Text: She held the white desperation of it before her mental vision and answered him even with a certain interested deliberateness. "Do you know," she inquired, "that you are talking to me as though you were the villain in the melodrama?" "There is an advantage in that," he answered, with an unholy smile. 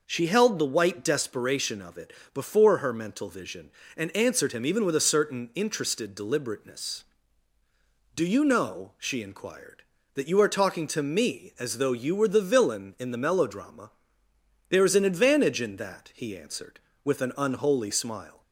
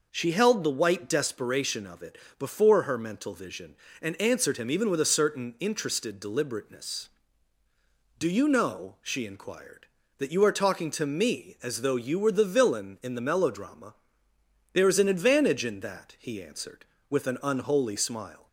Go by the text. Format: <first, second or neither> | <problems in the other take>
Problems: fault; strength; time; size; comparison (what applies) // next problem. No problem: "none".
neither | pauses between "it" and "before"; slight; the same in both